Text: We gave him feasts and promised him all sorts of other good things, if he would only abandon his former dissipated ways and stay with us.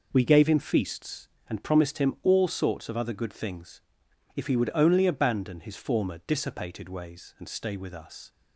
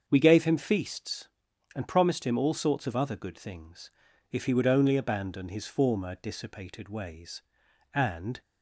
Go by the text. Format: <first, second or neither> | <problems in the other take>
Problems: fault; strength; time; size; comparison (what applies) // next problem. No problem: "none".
first | starts louder than the rest; until 1.0 s; 7 dB // stops before "stay with us"; at 8.4 s